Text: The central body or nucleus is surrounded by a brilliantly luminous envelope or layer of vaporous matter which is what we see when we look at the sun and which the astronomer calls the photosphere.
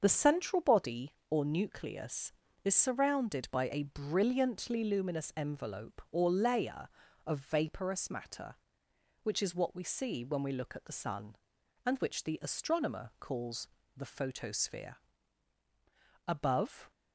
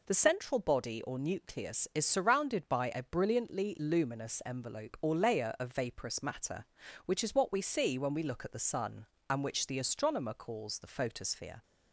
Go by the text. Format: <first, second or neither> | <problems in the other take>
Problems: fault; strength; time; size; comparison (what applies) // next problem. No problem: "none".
second | starts louder than the rest; until 1.0 s; 6.5 dB // pauses between "calls" and "the"; slight; at 13.6 s; 0.28 s long // goes on to say "Above"; noticeable; from 16.2 s on; 0.62 s long